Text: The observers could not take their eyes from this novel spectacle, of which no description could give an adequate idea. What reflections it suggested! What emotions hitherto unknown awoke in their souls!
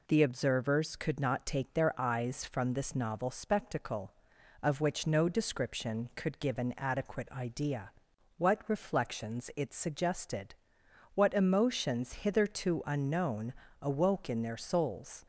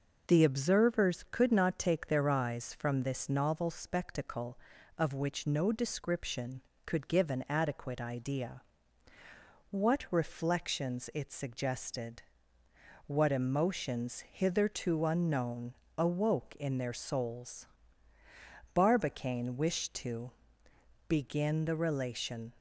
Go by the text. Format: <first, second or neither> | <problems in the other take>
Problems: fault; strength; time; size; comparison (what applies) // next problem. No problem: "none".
first | pauses between "unknown" and "awoke"; slight; at 15.7 s; 0.24 s long; slight in the first // goes on to say "Barbicane wished to begin the relation"; strong; from 18.7 s on; 3.8 s long